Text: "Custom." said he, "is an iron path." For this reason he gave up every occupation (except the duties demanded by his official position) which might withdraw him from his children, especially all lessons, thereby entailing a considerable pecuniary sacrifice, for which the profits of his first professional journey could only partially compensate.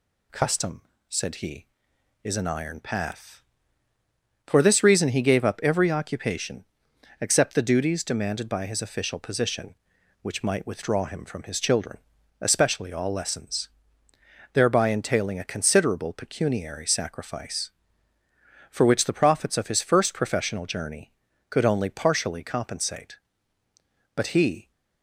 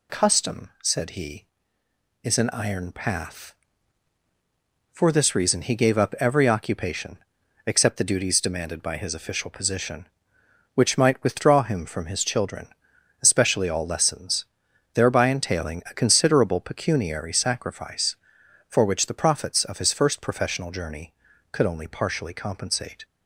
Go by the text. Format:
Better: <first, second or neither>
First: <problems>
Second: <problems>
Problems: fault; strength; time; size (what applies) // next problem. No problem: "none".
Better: second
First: goes on to say "But he"; from 24.1 s on; 0.56 s long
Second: none